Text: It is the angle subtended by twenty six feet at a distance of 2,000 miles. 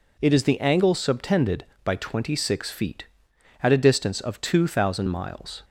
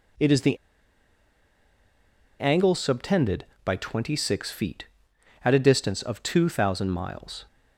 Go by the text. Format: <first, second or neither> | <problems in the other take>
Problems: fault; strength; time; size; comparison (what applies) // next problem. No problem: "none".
first | pauses between "the" and "angle"; strong; at 0.5 s; 1.8 s long